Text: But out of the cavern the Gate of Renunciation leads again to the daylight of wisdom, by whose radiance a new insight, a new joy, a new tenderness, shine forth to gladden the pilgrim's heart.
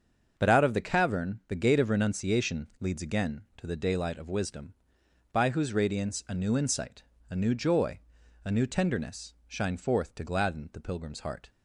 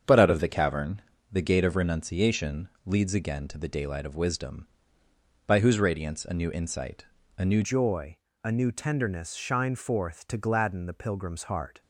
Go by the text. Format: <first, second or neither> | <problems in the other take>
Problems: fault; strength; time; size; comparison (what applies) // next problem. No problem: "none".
first | starts louder than the rest; strong; until 1.3 s; 7.5 dB; also in the first // pauses between "cavern" and "the"; slight; at 1.0 s; 0.32 s long // pauses between "Renunciation" and "leads"; slight; at 2.6 s; 0.16 s long // changes voice at "joy"; from 7.6 s on; 4.2 s long